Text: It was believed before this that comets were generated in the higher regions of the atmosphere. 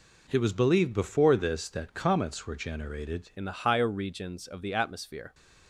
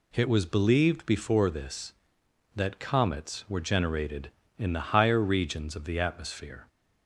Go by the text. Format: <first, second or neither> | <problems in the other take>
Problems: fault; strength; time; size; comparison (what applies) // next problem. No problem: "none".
second | changes voice at "in"; from 3.3 s on; 2.0 s long